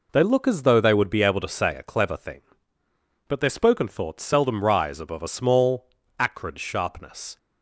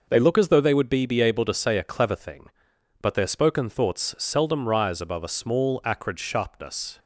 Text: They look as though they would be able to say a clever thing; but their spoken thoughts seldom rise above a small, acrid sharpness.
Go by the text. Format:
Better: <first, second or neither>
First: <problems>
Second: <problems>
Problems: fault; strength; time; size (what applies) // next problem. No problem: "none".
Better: first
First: none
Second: says "be" twice; at 1.0 s